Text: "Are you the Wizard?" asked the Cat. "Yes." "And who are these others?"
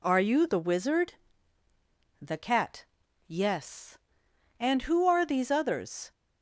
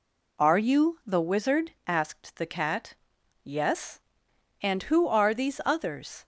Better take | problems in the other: second | skips "asked"; at 1.6 s

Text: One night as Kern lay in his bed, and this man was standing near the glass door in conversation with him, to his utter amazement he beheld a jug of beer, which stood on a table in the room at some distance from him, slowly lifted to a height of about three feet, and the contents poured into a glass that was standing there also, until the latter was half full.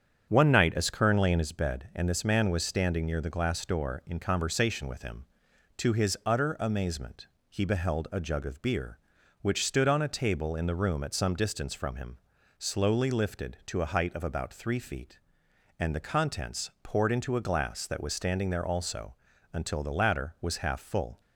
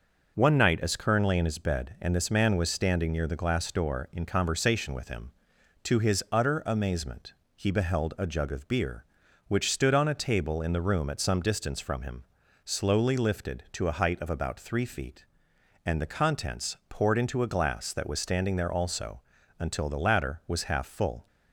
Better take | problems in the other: second | starts louder than the rest; strong; until 1.5 s; 8 dB // pauses between "amazement" and "he"; slight; at 7.2 s; 0.20 s long; slight in the second

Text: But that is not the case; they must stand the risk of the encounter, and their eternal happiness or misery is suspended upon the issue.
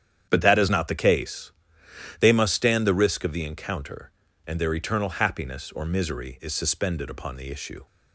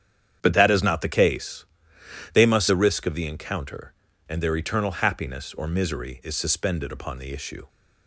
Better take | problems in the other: first | starts louder than the rest; strong; until 1.4 s; 9.5 dB; strong in the first // skips "stand"; at 2.6 s

